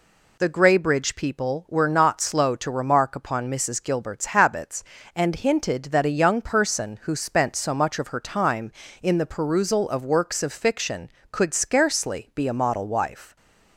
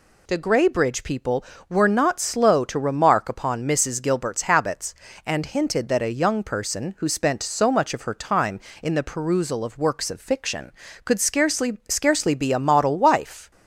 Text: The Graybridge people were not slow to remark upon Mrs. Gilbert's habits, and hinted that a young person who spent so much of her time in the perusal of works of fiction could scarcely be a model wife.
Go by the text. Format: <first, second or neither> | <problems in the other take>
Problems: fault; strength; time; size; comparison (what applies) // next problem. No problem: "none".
first | says "scarcely" twice; at 11.8 s